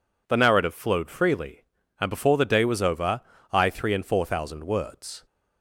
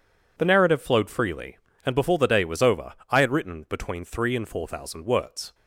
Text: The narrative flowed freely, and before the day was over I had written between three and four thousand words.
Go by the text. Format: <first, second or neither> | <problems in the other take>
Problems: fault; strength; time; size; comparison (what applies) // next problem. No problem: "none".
second | pauses between "over" and "I"; slight; at 3.2 s; 0.30 s long; slight in the second // skips "had written between"; at 3.6 s